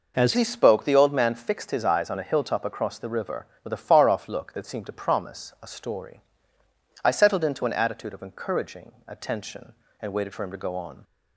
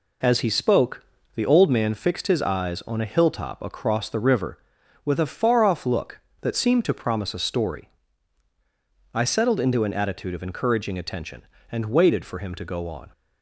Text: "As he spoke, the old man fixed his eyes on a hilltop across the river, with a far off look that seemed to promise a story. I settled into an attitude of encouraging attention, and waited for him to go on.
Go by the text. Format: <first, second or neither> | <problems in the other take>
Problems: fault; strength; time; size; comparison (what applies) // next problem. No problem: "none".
second | changes voice at "he"; from 0.3 s on; 10.7 s long // pauses between "encouraging" and "attention"; slight; at 8.9 s; 0.16 s long